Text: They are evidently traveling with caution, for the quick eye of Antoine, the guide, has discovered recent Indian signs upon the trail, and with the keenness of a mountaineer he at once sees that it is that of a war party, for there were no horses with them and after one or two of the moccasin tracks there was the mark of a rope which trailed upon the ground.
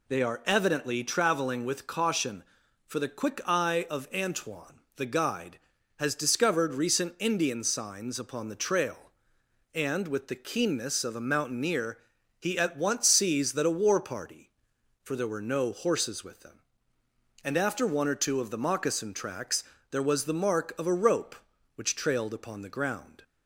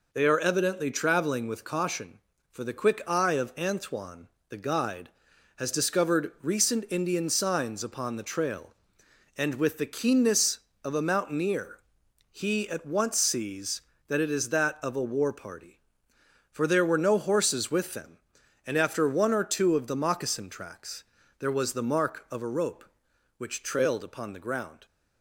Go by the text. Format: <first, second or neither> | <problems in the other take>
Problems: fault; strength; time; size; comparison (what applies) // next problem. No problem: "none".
second | pauses between "mountaineer" and "he"; at 11.9 s; 0.42 s long; noticeable in the second // skips "it is that of"; at 13.6 s // pauses between "tracks" and "there"; slight; at 19.6 s; 0.30 s long; slight in the second